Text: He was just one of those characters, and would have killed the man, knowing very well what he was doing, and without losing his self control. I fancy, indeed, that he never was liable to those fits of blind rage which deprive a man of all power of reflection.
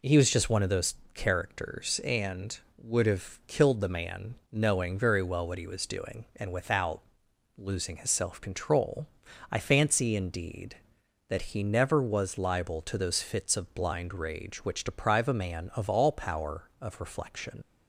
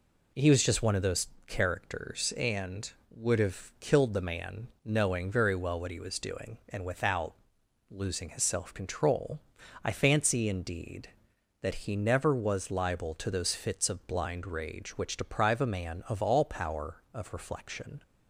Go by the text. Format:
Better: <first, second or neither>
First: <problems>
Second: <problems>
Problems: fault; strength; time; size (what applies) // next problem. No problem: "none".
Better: second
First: pauses between "those" and "characters"; slight; at 0.9 s; 0.20 s long // pauses between "without" and "losing"; noticeable; at 7.0 s; 0.56 s long // leaves "reflection" unfinished; at 17.6 s; 75 ms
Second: pauses between "those" and "characters"; slight; at 1.2 s; 0.20 s long // pauses between "without" and "losing"; noticeable; at 7.3 s; 0.56 s long